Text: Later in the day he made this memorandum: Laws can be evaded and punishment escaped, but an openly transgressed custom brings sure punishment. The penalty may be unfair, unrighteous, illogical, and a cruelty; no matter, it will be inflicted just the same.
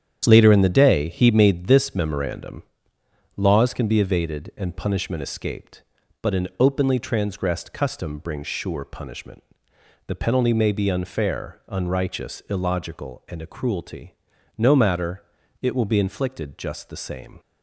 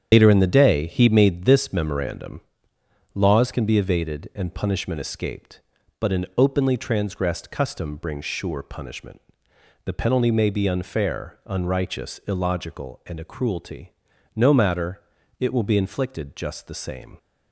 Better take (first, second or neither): first